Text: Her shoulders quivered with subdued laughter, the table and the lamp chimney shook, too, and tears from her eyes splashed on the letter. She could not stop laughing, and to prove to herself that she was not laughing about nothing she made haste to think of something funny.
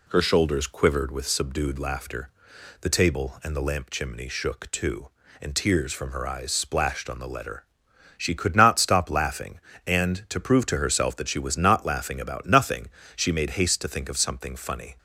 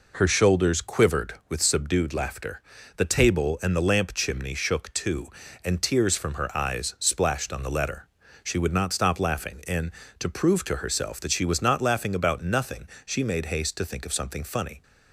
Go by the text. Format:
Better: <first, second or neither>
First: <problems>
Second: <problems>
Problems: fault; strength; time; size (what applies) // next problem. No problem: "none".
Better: first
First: pauses between "nothing" and "she"; slight; at 12.8 s; 0.28 s long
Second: says "would" for "could"; at 8.5 s // pauses between "nothing" and "she"; slight; at 12.8 s; 0.18 s long